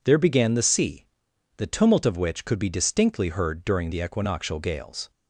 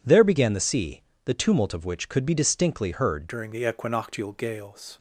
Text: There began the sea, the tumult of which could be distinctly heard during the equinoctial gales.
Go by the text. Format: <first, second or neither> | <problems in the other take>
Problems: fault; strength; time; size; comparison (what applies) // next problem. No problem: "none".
first | changes voice at "during"; from 3.2 s on; 1.7 s long